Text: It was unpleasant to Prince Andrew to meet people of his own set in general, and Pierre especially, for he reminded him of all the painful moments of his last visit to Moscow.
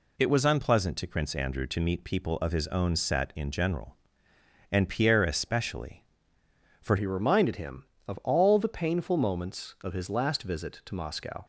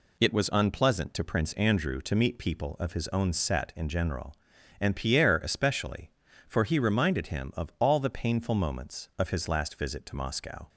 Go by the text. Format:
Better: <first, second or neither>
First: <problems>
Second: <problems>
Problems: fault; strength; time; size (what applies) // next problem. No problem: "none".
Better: second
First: changes voice at "he"; from 6.9 s on; 4.5 s long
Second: none